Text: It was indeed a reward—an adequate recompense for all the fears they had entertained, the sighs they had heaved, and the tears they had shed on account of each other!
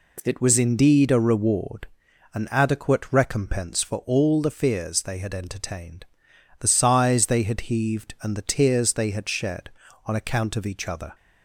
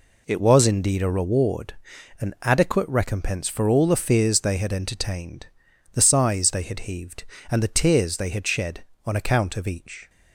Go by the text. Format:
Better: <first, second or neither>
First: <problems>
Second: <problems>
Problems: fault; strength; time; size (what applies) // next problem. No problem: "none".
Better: first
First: none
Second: stops before "other"; at 10.0 s